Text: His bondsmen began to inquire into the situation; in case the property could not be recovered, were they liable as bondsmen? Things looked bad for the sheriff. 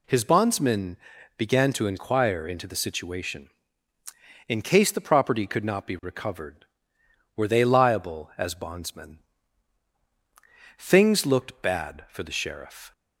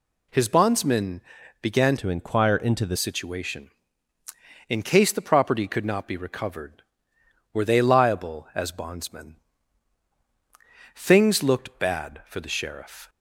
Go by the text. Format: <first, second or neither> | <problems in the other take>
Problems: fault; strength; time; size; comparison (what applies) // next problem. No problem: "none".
first | pauses between "bondsmen" and "began"; at 1.2 s; 0.40 s long; also in the first // changes voice from "to" to "the"; from 1.9 to 2.9 s; 1.0 s long